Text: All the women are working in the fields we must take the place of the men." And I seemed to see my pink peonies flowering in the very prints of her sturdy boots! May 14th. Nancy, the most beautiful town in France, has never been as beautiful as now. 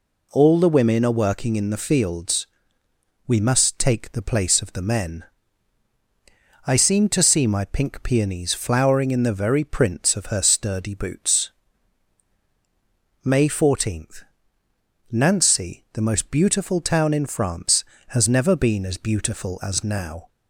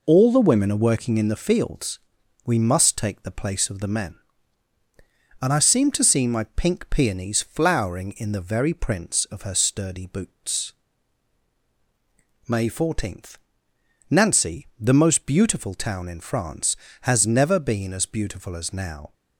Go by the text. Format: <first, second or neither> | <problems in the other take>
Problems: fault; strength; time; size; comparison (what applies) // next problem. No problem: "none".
second | pauses between "fields" and "we"; noticeable; at 2.4 s; 0.82 s long; noticeable in the second // skips "And"; at 5.9 s